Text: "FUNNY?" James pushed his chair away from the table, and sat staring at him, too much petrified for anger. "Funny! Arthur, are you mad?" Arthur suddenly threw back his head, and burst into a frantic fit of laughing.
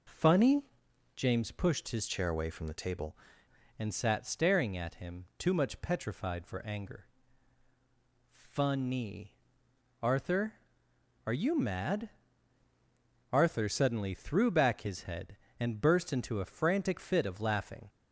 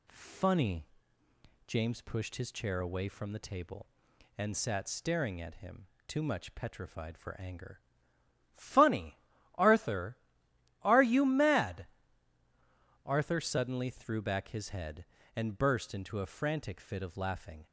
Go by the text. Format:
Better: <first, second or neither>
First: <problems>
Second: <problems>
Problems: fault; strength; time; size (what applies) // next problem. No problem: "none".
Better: second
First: changes voice from "chair" to "table"; from 2.0 to 3.1 s; 1.1 s long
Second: none